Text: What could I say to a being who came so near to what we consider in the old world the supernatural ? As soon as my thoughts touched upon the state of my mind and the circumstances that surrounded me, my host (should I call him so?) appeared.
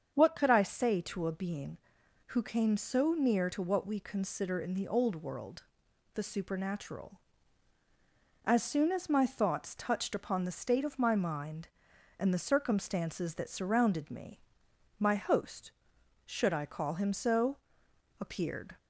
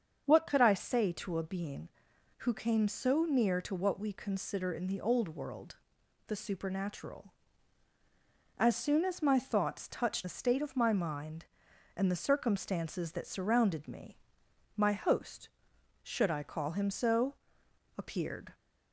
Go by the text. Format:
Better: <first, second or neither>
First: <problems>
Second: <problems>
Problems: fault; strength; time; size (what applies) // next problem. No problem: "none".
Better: first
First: starts louder than the rest; strong; until 1.1 s; 7 dB // pauses between "world" and "the"; noticeable; at 5.6 s; 0.50 s long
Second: starts louder than the rest; until 1.2 s; 7 dB // pauses between "world" and "the"; noticeable; at 5.7 s; 0.50 s long // skips "upon"; at 10.2 s